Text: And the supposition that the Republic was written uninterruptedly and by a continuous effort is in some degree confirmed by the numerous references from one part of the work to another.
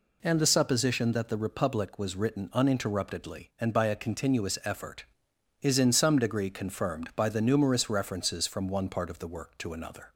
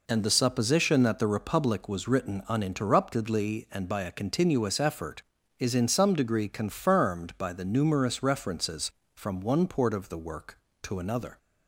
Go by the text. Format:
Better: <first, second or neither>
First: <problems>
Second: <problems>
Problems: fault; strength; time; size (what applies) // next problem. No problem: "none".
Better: first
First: none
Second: says "port" for "part"; at 9.6 s